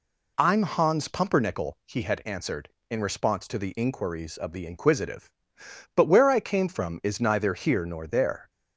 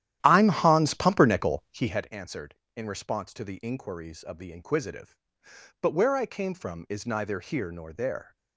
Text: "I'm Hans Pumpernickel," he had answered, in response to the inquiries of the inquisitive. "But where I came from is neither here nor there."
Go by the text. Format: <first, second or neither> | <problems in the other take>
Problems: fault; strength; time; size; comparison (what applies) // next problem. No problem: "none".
first | starts louder than the rest; strong; until 2.1 s; 12 dB